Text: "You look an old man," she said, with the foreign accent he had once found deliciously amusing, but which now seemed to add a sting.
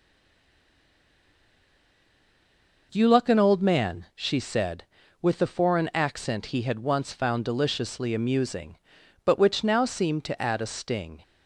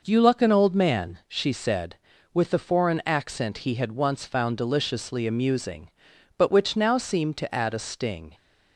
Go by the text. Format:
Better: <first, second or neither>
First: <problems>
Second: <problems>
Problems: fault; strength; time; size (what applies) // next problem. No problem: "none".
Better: second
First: stays silent before the first word; strong; until 2.9 s; 2.9 s long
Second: none